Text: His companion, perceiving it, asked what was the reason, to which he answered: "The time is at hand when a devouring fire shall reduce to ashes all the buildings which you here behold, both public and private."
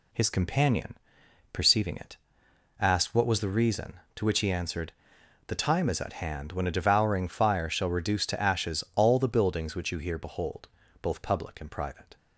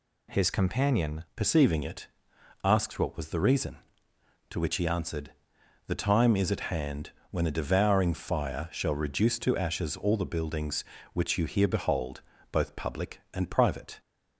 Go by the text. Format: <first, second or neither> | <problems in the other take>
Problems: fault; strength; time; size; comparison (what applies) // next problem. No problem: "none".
first | changes voice at "perceiving"; from 1.3 s on; 12.6 s long // pauses between "hand" and "when"; slight; at 7.1 s; 0.18 s long